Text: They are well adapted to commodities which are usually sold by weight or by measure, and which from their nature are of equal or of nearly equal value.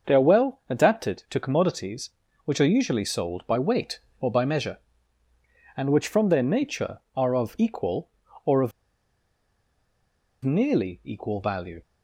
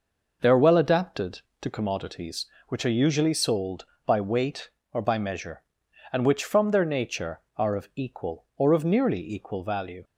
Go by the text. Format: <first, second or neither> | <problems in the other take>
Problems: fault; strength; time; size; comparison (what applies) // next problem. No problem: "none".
second | starts louder than the rest; until 1.1 s; 6.5 dB // pauses between "of" and "nearly"; strong; at 8.7 s; 1.7 s long